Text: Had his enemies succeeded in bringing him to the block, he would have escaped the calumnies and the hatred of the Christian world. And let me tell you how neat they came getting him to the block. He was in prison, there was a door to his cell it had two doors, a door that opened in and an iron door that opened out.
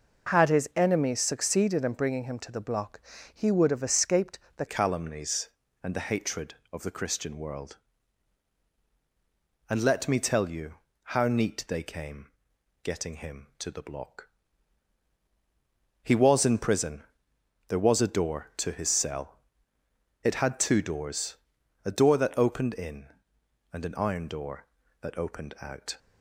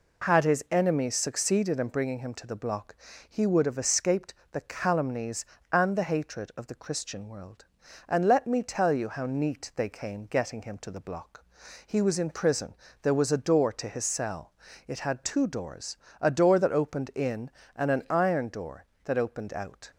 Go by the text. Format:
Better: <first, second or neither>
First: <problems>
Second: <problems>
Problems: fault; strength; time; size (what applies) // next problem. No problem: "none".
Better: second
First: pauses between "escaped" and "the"; slight; at 4.3 s; 0.18 s long // changes voice at "calumnies"; from 4.6 s on; 21.3 s long // pauses between "you" and "how"; slight; at 10.7 s; 0.36 s long // pauses between "came" and "getting"; noticeable; at 12.2 s; 0.56 s long // pauses between "cell" and "it"; noticeable; at 19.3 s; 0.84 s long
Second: pauses between "escaped" and "the"; slight; at 4.3 s; 0.18 s long // pauses between "cell" and "it"; slight; at 14.5 s; 0.34 s long